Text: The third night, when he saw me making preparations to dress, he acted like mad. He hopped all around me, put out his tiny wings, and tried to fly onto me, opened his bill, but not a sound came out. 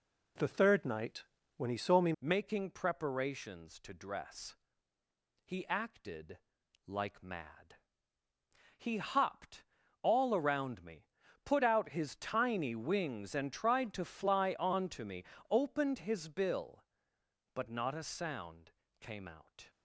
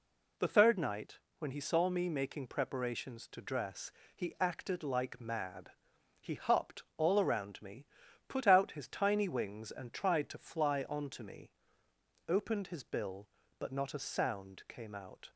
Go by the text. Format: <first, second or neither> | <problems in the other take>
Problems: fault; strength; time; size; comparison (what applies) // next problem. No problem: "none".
second | changes voice at "making"; from 2.1 s on; 17.5 s long // pauses between "acted" and "like"; noticeable; at 6.3 s; 0.46 s long // pauses between "hopped" and "all"; at 9.6 s; 0.38 s long // pauses between "sound" and "came"; slight; at 18.7 s; 0.28 s long